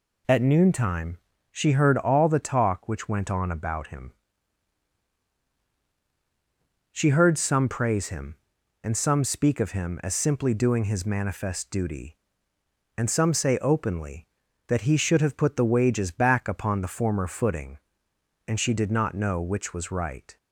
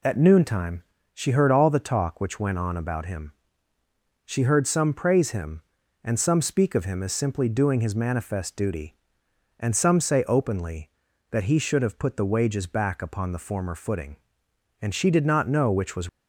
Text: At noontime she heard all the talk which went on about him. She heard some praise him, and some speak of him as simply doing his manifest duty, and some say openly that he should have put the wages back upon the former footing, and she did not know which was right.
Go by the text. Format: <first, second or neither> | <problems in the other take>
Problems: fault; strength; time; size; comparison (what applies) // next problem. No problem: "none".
first | pauses between "noontime" and "she"; slight; at 0.8 s; 0.32 s long; slight in the first // stops before "right"; at 16.0 s